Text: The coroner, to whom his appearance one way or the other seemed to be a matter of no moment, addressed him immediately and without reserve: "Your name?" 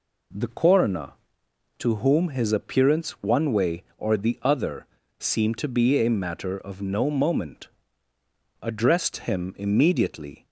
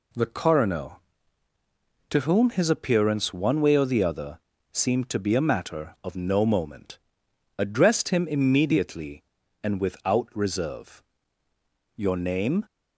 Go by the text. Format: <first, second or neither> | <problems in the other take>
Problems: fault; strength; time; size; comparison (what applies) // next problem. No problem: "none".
second | pauses between "other" and "seemed"; slight; at 4.8 s; 0.34 s long; slight in the second // stops before "and without reserve Your name"; at 10.4 s